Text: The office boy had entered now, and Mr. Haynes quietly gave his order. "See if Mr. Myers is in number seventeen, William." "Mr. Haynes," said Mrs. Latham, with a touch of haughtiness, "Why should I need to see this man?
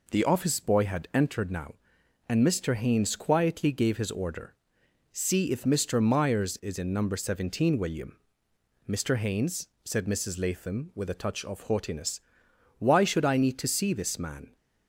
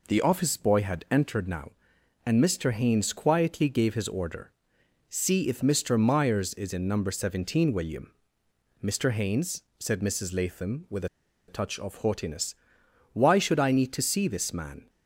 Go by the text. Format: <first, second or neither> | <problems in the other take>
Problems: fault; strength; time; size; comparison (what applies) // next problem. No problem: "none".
first | pauses between "with" and "a"; at 11.0 s; 0.42 s long